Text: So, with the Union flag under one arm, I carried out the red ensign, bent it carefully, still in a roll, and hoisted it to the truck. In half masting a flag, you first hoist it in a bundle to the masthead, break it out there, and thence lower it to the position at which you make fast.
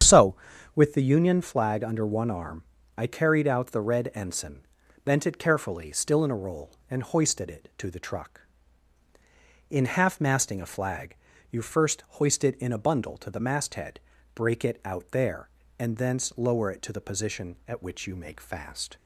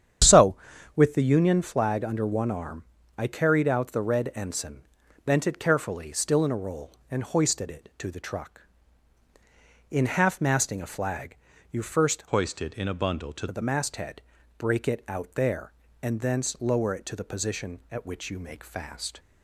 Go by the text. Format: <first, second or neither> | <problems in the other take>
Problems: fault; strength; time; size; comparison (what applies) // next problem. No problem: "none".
first | starts louder than the rest; strong; until 1.6 s; 9 dB; strong in the first // changes voice from "hoist" to "to"; from 12.2 to 13.4 s; 1.2 s long